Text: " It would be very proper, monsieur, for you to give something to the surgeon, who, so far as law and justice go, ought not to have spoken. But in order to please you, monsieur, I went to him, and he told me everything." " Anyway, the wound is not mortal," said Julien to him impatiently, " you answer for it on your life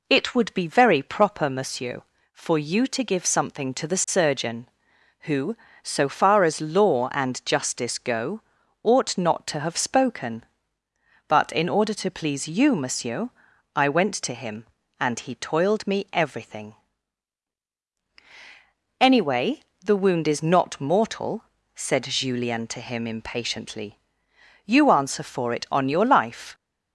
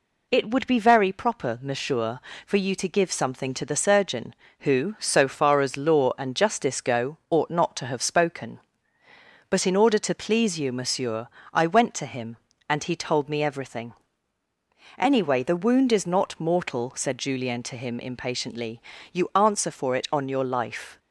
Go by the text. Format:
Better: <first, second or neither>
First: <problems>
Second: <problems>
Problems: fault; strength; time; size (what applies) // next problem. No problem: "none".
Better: second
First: says "toiled" for "told"; at 15.3 s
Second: none